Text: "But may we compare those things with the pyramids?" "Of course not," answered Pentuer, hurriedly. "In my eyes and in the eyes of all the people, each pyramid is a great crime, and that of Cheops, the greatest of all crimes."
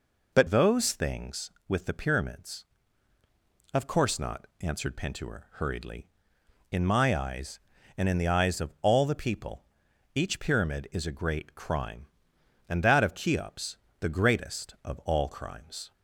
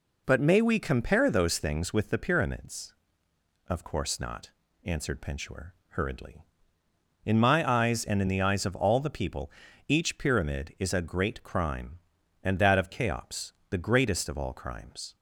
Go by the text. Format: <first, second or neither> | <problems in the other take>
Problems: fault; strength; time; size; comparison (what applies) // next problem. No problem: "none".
second | skips "may we compare"; at 0.4 s